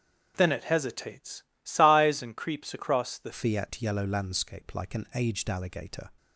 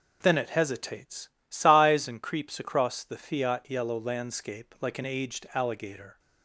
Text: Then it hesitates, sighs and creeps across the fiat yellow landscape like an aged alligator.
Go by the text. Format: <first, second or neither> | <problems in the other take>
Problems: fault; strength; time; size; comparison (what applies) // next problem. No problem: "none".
second | starts louder than the rest; until 1.3 s; 7 dB // changes voice at "fiat"; from 3.3 s on; 2.7 s long